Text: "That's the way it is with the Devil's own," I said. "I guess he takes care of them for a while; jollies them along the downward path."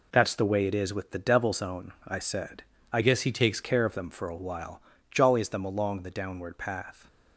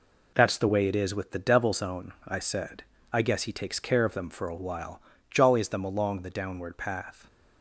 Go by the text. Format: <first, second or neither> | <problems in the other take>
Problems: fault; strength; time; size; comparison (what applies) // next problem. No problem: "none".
second | changes voice from "guess" to "takes"; from 3.0 to 3.6 s; 0.6 s long